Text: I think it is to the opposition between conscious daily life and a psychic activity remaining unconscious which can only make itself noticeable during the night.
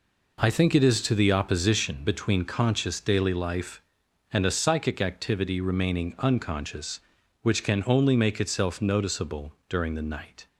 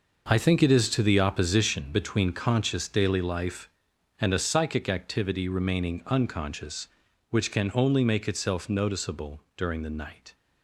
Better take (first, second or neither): first